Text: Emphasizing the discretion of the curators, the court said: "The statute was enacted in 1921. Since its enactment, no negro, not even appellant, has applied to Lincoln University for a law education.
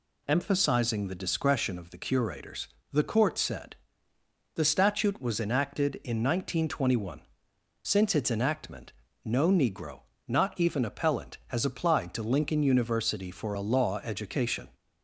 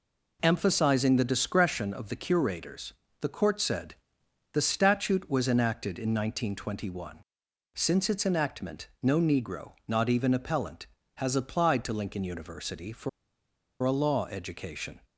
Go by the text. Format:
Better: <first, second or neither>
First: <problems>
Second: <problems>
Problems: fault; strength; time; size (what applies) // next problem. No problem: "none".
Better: first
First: none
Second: pauses between "for" and "a"; noticeable; at 13.0 s; 0.73 s long